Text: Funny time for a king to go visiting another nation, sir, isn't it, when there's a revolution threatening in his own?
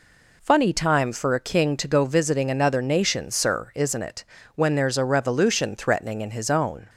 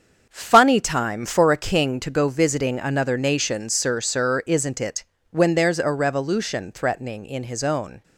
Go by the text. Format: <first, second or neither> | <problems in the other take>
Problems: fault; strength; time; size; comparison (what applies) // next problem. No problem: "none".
first | starts louder than the rest; until 1.2 s; 7 dB // says "sir" twice; at 3.9 s